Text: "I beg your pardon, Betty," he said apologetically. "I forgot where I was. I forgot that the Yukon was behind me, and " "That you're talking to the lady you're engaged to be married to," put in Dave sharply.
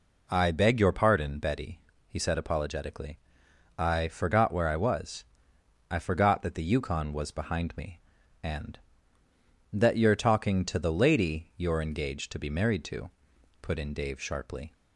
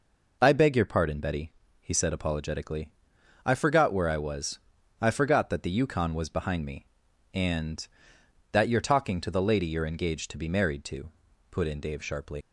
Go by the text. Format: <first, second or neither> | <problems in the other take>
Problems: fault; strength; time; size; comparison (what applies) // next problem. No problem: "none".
first | leaves "sharply" unfinished; at 12.4 s; 70 ms